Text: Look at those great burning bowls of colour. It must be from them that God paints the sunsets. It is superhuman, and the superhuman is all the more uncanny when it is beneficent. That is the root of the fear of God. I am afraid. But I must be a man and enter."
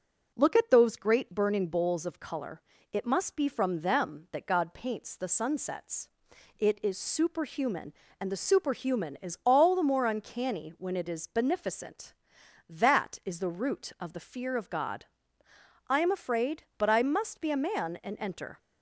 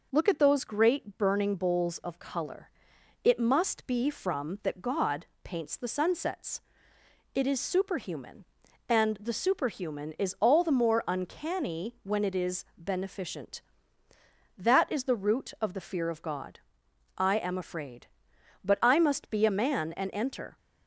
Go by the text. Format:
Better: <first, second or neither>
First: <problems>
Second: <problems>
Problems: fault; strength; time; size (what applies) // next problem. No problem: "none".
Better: first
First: none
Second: skips "them"; at 4.6 s // pauses between "God" and "paints"; slight; at 5.2 s; 0.18 s long